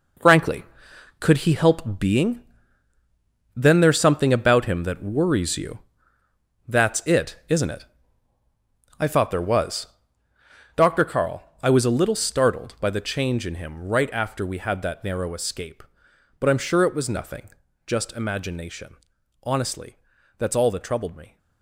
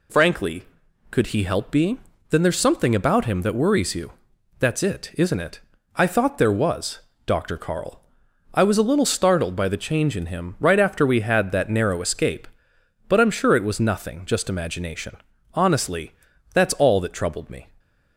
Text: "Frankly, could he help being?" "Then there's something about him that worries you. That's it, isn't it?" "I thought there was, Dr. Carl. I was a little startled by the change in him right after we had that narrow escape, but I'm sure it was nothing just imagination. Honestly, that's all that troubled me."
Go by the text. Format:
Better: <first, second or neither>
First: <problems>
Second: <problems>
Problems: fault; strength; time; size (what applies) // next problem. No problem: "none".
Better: second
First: gets quieter; strong; throughout; 9.5 dB // pauses between "nothing" and "just"; slight; at 17.4 s; 0.36 s long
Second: none